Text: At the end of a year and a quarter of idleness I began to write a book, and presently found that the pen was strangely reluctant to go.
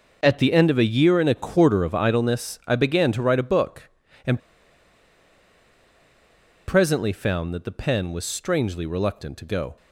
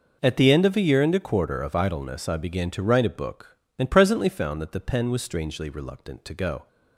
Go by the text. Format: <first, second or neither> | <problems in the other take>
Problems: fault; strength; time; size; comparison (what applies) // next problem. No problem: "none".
second | pauses between "and" and "presently"; strong; at 4.3 s; 2.2 s long